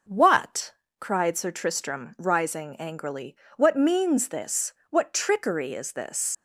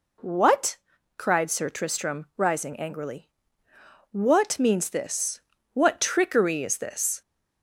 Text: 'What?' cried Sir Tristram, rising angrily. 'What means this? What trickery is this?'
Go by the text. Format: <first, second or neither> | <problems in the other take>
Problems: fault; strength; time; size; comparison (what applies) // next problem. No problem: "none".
second | leaves "this" unfinished; at 6.3 s; 100 ms